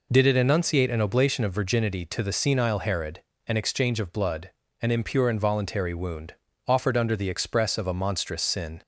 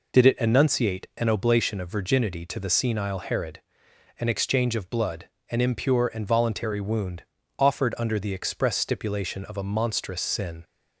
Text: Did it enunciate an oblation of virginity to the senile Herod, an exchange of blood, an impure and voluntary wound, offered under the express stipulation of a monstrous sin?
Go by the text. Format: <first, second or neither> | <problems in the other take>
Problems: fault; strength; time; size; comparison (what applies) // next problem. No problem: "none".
second | skips "stipulation"; at 7.7 s